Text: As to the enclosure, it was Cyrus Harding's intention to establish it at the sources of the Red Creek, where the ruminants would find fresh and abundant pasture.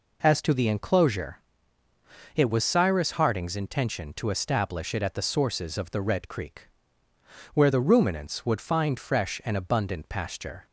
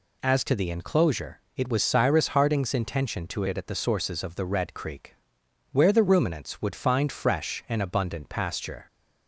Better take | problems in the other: first | skips "establish"; at 3.4 s

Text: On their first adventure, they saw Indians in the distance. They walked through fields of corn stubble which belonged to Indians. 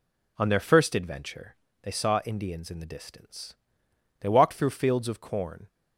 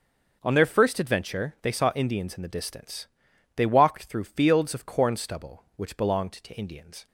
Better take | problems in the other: second | stops before "stubble which belonged to Indians"; at 5.6 s

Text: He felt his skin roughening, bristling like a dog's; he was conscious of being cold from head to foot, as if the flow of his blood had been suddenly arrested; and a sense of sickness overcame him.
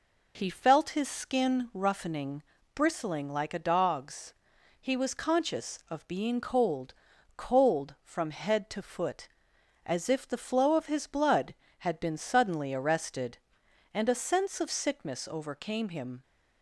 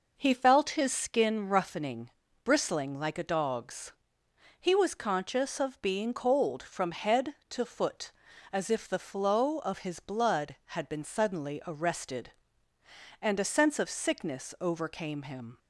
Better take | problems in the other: second | says "cold" twice; at 7.3 s

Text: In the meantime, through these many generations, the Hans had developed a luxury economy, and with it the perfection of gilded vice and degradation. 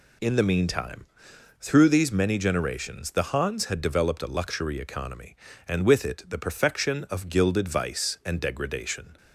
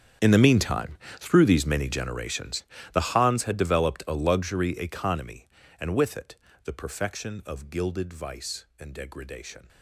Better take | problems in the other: first | gets quieter; strong; throughout; 17.5 dB // pauses between "it" and "the"; slight; at 6.3 s; 0.28 s long

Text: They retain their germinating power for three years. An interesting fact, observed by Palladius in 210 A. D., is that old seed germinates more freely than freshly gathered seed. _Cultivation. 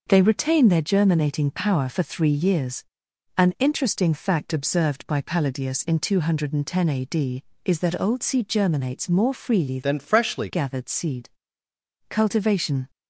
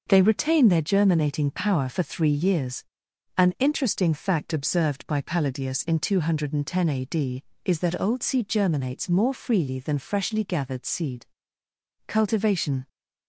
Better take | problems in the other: second | changes voice from "than" to "freshly"; from 9.8 to 10.4 s; 0.6 s long

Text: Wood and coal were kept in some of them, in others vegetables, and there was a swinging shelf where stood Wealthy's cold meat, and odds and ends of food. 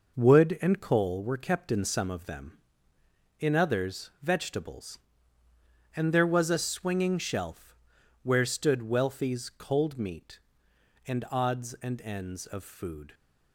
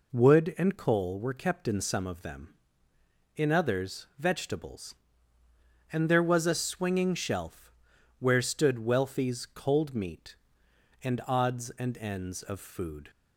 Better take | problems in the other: second | gets quieter; throughout; 6.5 dB // pauses between "shelf" and "where"; noticeable; at 7.7 s; 0.46 s long; noticeable in the second

